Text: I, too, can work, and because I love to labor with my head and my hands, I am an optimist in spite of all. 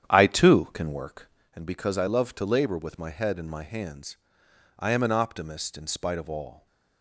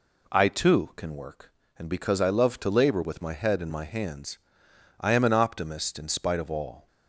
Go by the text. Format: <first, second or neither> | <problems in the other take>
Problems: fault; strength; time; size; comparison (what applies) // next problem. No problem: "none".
second | starts louder than the rest; strong; until 1.6 s; 9.5 dB